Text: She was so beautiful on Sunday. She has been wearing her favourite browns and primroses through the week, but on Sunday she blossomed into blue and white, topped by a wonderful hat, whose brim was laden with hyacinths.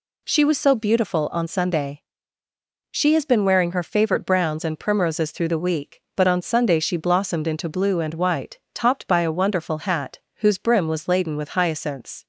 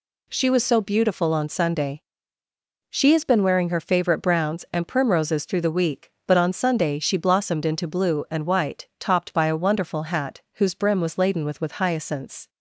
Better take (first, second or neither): first